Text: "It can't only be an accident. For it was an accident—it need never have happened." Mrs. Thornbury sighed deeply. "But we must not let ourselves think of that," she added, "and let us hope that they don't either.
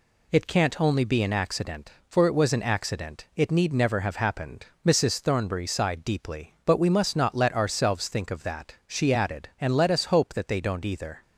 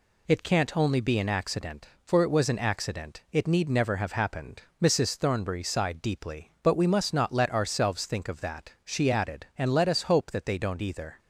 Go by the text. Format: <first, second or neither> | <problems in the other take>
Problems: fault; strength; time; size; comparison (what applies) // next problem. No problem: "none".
neither | none